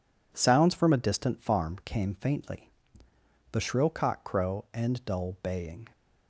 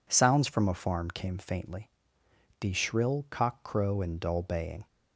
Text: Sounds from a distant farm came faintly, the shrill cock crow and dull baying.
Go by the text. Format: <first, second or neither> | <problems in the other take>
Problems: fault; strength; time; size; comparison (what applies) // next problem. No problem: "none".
first | skips "distant"; at 0.7 s